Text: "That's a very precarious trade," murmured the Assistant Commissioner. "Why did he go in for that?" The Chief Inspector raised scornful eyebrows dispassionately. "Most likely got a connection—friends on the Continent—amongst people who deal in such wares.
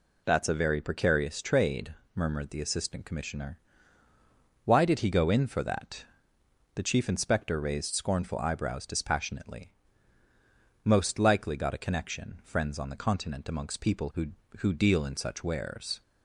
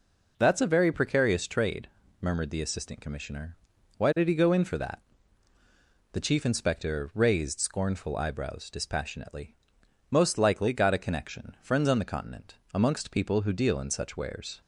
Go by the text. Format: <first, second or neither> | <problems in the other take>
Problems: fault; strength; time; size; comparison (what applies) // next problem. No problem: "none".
second | says "who" twice; at 14.5 s